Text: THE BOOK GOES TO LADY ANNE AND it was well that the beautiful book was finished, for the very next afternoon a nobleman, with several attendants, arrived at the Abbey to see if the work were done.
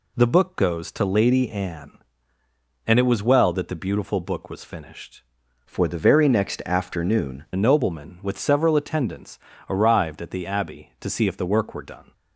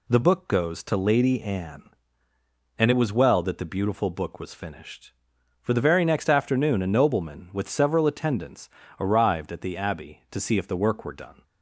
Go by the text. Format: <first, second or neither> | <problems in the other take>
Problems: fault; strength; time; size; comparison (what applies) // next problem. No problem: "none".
second | changes voice from "for" to "afternoon"; from 5.6 to 7.4 s; 1.8 s long